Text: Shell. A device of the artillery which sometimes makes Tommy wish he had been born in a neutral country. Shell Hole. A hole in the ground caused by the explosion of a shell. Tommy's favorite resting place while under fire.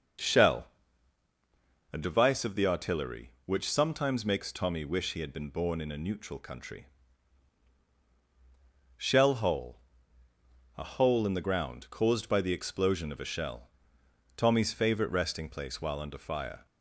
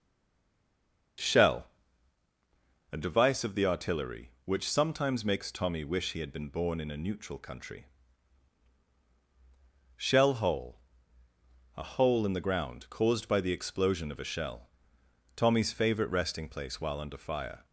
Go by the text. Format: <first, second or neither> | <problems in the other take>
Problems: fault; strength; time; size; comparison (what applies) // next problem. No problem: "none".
first | stays silent before the first word; until 1.1 s; 1.1 s long // starts louder than the rest; until 3.4 s; 6.5 dB; also in the first